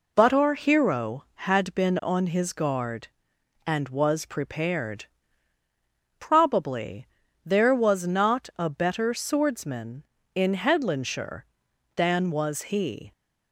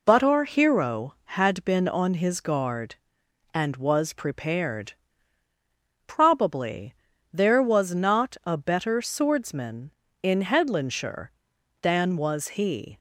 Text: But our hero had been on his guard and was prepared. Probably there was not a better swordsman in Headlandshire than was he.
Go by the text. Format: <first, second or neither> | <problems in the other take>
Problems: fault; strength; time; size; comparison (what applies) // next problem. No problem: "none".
neither | pauses between "Probably" and "there"; the same in both